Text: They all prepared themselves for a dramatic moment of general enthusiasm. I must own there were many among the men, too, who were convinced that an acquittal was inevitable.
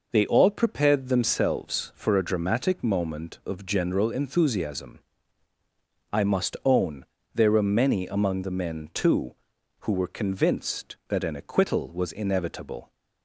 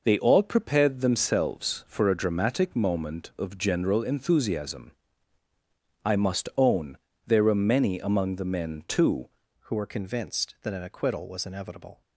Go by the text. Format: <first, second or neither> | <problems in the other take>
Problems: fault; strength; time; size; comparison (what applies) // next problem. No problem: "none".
first | pauses between "own" and "there"; slight; at 6.9 s; 0.28 s long; slight in the first // changes voice at "who"; from 9.6 s on; 2.4 s long